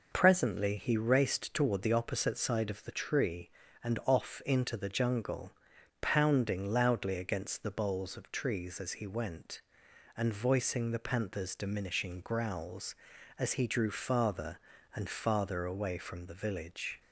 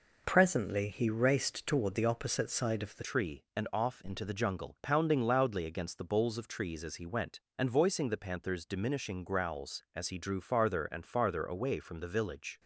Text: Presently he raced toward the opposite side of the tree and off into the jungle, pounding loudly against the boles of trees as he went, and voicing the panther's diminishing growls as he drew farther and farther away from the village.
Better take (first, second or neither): first